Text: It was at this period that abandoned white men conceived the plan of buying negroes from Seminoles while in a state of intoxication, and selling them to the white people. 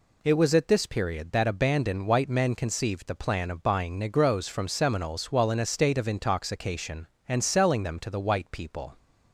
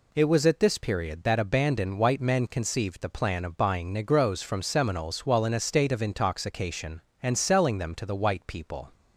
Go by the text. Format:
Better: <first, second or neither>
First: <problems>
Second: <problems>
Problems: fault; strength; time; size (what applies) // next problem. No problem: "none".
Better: neither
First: none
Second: none